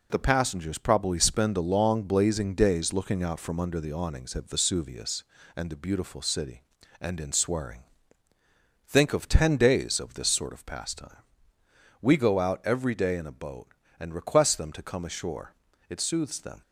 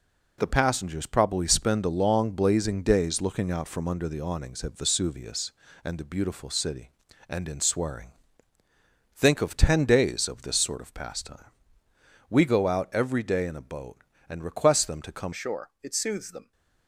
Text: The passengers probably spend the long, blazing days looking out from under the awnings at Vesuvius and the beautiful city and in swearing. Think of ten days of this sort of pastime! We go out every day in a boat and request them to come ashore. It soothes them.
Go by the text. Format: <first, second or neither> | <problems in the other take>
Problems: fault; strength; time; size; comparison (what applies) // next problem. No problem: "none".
first | changes voice at "ashore"; from 15.3 s on; 1.2 s long